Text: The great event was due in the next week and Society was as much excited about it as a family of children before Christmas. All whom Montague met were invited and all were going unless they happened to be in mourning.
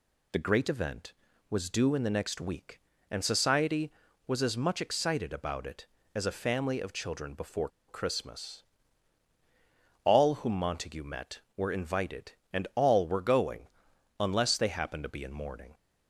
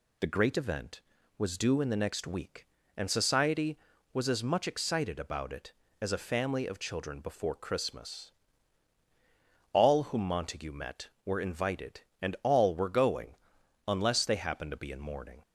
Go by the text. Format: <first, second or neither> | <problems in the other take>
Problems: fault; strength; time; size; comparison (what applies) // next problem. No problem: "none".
second | pauses between "before" and "Christmas"; slight; at 7.6 s; 0.20 s long // pauses between "going" and "unless"; noticeable; at 13.6 s; 0.52 s long; noticeable in the second